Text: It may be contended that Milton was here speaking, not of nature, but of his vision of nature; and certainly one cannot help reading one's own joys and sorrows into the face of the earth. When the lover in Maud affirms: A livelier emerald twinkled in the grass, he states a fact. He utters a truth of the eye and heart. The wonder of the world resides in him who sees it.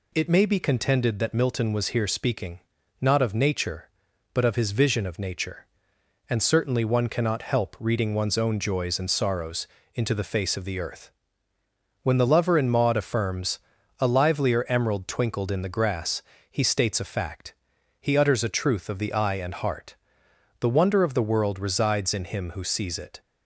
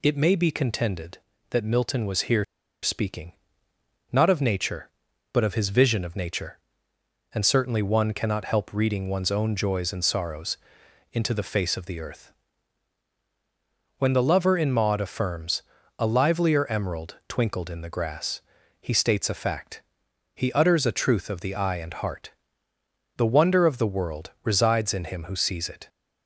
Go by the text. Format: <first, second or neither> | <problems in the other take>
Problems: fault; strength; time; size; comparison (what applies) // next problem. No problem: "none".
first | pauses between "here" and "speaking"; at 2.4 s; 0.38 s long // pauses between "sorrows" and "into"; noticeable; at 10.5 s; 0.54 s long; slight in the first